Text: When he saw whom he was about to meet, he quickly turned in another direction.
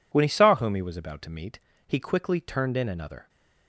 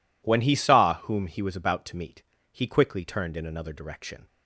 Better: second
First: stops before "direction"; at 3.2 s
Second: none

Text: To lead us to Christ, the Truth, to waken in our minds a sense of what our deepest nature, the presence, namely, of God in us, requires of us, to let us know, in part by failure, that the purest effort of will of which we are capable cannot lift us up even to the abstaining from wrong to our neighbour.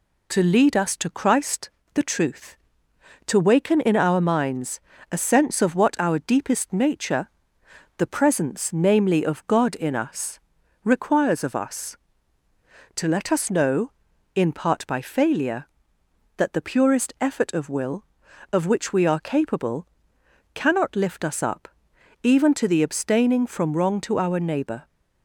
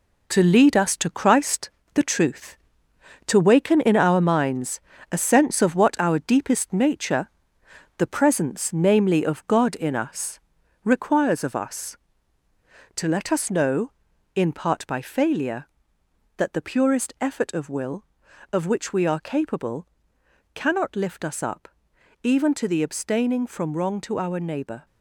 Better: first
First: pauses between "minds" and "a"; slight; at 4.7 s; 0.32 s long // pauses between "capable" and "cannot"; noticeable; at 19.8 s; 0.68 s long // pauses between "up" and "even"; noticeable; at 21.6 s; 0.56 s long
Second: gets quieter; strong; throughout; 7 dB // pauses between "minds" and "a"; slight; at 4.7 s; 0.32 s long // pauses between "capable" and "cannot"; noticeable; at 19.8 s; 0.68 s long // pauses between "up" and "even"; noticeable; at 21.6 s; 0.56 s long

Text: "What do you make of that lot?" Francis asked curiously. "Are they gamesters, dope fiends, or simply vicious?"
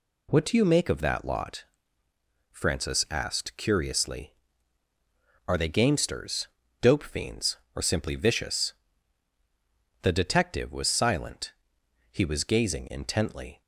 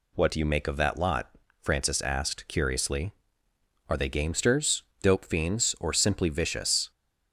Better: second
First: goes on to say "The detective was silent He was gazing intently"; strong; from 10.0 s on; 3.5 s long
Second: none

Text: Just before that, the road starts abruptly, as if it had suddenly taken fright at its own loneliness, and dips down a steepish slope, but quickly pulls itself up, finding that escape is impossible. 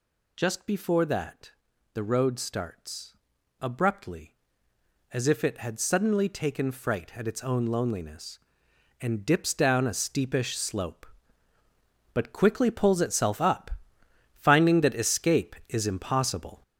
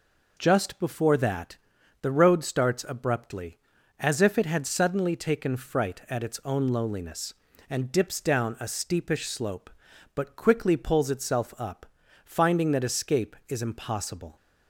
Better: second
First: gets louder; noticeable; throughout; 6 dB // pauses between "starts" and "abruptly"; noticeable; at 3.1 s; 0.46 s long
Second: none

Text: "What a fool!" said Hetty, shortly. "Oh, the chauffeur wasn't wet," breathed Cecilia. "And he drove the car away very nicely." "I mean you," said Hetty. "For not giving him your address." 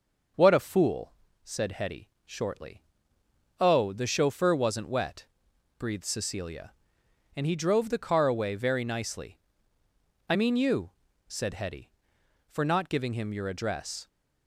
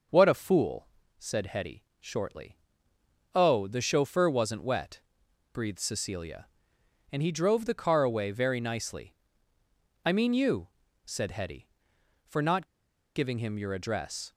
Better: first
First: none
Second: pauses between "not" and "giving"; noticeable; at 12.6 s; 0.50 s long

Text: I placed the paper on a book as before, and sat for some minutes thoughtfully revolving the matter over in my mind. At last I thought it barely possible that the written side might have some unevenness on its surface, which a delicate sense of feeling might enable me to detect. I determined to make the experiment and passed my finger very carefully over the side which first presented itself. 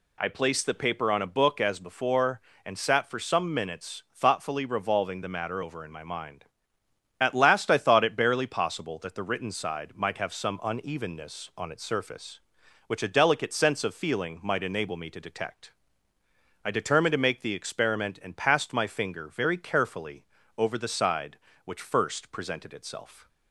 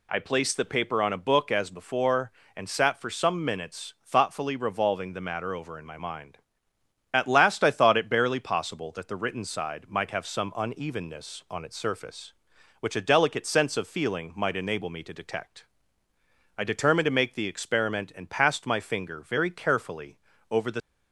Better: first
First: pauses between "carefully" and "over"; slight; at 20.2 s; 0.32 s long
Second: pauses between "carefully" and "over"; slight; at 20.1 s; 0.32 s long // stops before "side which first presented itself"; at 20.8 s

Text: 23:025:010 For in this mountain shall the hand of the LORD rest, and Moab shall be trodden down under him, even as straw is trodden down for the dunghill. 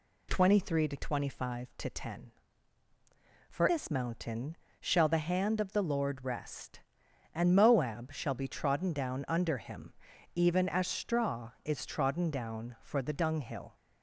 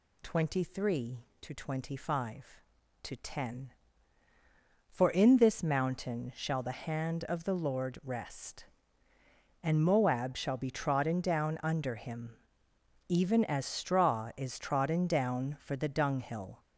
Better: second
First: skips "in"; at 3.6 s // pauses between "mountain" and "shall"; slight; at 4.5 s; 0.24 s long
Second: none

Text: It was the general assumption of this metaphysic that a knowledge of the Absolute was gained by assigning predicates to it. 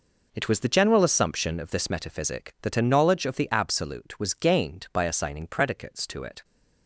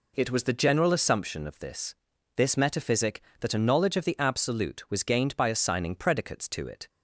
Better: first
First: none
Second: says "this" twice; at 2.3 s

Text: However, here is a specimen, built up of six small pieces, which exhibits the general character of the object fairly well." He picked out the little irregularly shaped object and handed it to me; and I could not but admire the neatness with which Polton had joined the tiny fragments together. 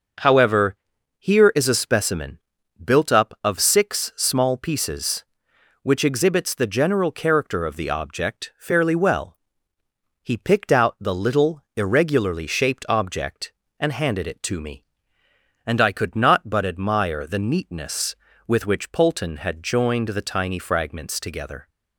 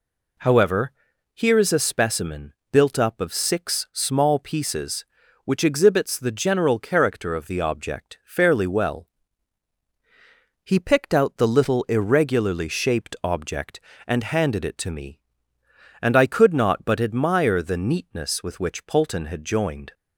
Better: first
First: none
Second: stops before "the tiny fragments together"; at 19.9 s

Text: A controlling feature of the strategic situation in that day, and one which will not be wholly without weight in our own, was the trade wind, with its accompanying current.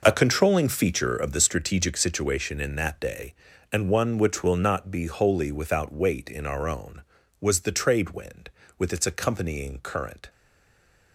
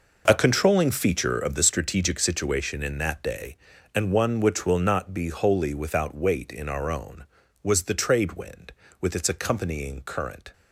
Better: second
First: stays silent after the last word; slight; from 10.2 s on; 0.9 s long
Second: none

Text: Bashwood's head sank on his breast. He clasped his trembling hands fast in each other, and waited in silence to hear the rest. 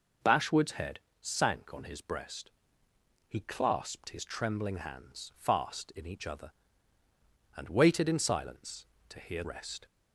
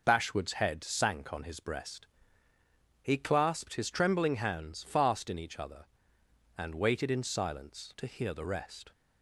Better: second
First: pauses between "head" and "sank"; slight; at 1.0 s; 0.20 s long // skips "the"; at 9.4 s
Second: none

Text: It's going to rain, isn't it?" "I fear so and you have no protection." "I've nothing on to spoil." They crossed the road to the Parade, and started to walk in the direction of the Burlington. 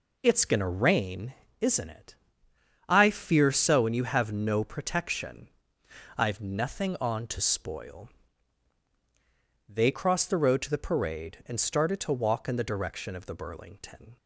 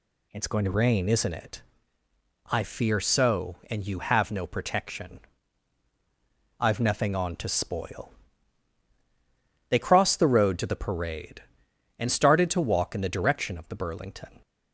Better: second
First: starts louder than the rest; noticeable; until 1.5 s; 4 dB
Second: none

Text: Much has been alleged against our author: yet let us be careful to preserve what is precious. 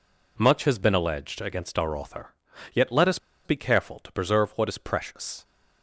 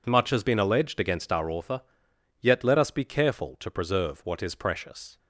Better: second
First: pauses between "us" and "be"; slight; at 3.1 s; 0.28 s long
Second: none

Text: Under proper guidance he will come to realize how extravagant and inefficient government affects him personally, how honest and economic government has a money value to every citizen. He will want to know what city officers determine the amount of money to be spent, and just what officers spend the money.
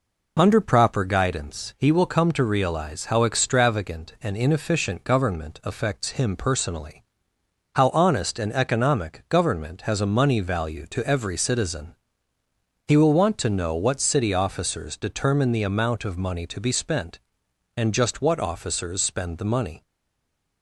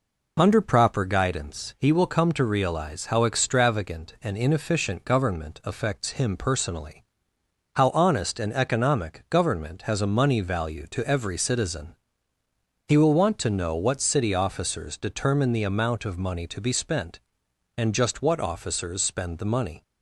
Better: second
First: stays silent after the last word; slight; from 19.8 s on; 0.8 s long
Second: none

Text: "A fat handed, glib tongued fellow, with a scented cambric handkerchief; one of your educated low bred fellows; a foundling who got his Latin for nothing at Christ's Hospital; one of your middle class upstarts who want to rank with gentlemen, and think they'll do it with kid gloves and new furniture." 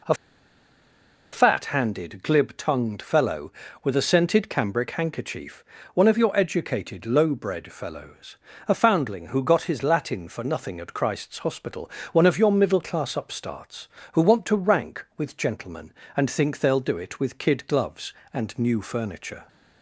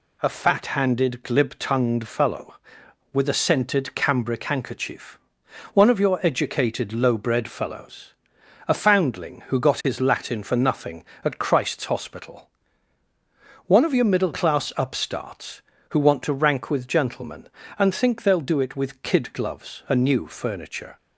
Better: second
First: pauses between "A" and "fat"; at 0.1 s; 1.1 s long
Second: none

